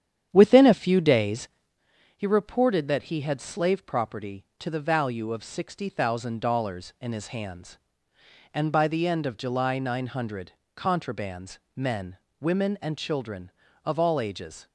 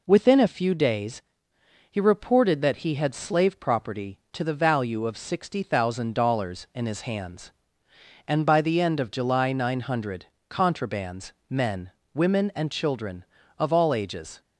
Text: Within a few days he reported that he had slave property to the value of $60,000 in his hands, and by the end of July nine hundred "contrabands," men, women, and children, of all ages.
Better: second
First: starts louder than the rest; strong; until 1.9 s; 9.5 dB // pauses between "days" and "he"; noticeable; at 1.4 s; 0.68 s long // pauses between "hundred" and "contrabands"; slight; at 10.5 s; 0.24 s long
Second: pauses between "days" and "he"; noticeable; at 1.2 s; 0.68 s long // pauses between "hundred" and "contrabands"; slight; at 10.2 s; 0.24 s long

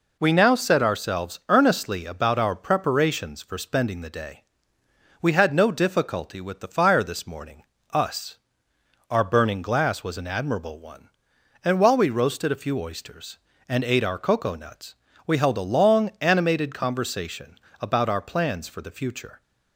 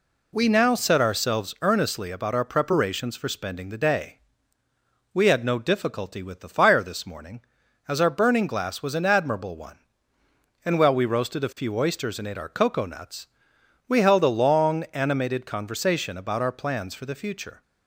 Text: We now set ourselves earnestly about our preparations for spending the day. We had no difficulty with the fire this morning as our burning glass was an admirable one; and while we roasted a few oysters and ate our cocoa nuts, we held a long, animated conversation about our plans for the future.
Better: second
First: says "us" for "as"; at 7.9 s // pauses between "conversation" and "about"; slight; at 17.5 s; 0.22 s long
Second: none

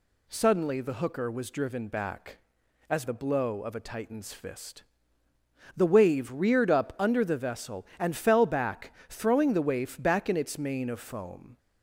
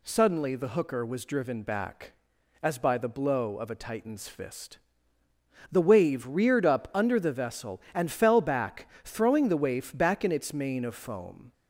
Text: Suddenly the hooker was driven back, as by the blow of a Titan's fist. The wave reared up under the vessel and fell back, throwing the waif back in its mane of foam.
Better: second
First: skips "by"; at 3.0 s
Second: none

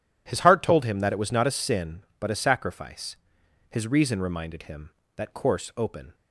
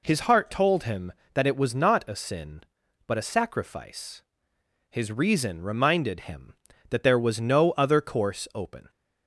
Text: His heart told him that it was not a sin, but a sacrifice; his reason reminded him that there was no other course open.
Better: second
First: skips "there was no other"; at 5.3 s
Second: none

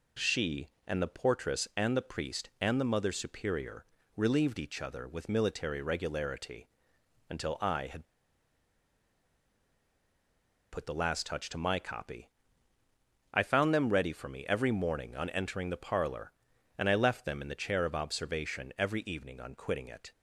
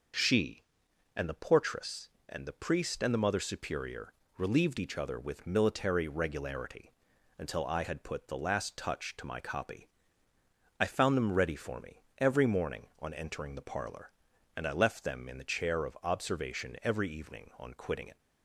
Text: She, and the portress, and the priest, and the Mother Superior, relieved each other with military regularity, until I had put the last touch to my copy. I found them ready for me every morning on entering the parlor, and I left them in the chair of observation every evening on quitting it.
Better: second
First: pauses between "had" and "put"; strong; at 8.0 s; 2.6 s long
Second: none

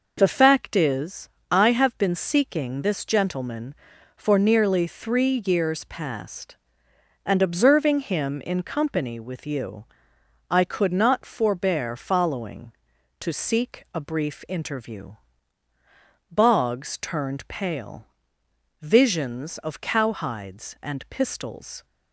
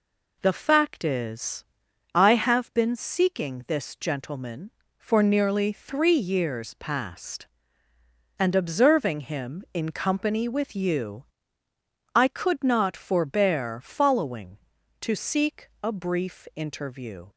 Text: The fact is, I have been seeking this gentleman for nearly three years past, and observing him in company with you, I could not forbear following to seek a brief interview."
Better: second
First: goes on to say "Boggs turned pale Visions of cowhides and pistols"; strong; from 16.3 s on; 5.5 s long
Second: none

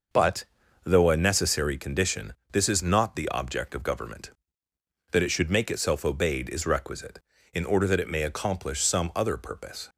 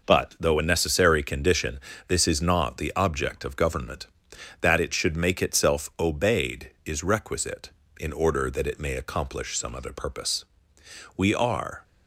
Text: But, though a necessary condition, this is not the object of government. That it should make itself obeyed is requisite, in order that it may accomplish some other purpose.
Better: first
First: none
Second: goes on to say "We are"; noticeable; from 11.1 s on; 0.66 s long

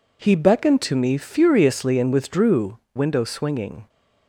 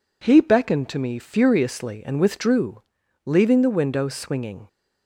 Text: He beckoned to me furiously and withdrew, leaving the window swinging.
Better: second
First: skips "leaving the"; at 2.8 s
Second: none

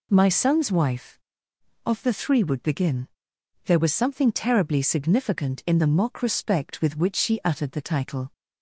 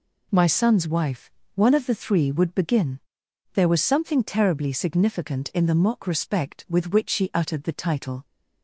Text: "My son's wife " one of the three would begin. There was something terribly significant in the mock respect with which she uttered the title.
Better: second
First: skips "one"; at 1.8 s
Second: none

